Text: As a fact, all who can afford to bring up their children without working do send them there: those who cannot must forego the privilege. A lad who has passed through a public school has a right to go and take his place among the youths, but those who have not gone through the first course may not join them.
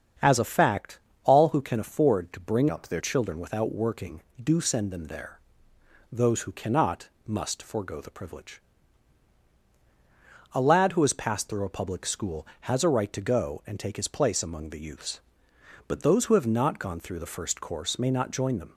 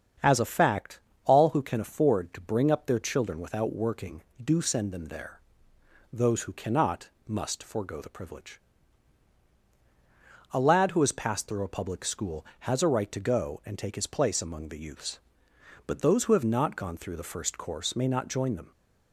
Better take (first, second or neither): second